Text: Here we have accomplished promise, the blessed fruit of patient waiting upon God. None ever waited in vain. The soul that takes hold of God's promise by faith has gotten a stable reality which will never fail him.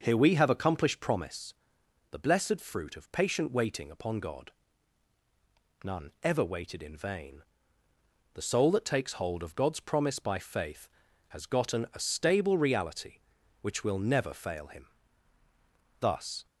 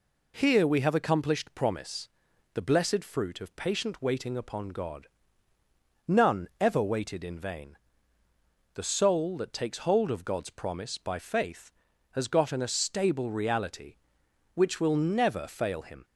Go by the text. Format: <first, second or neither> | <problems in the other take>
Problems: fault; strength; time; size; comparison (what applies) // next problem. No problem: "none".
second | starts louder than the rest; noticeable; until 1.0 s; 6 dB // goes on to say "Thus"; slight; from 15.9 s on; 0.46 s long